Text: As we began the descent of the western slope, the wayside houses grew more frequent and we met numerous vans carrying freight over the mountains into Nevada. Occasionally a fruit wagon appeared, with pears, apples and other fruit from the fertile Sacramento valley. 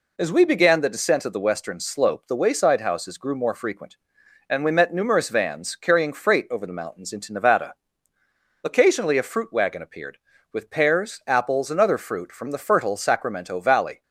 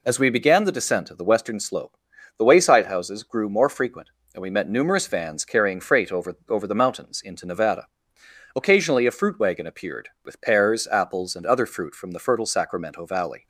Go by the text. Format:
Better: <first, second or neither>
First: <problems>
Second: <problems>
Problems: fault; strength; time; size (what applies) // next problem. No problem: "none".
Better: first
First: none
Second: says "over" twice; at 6.4 s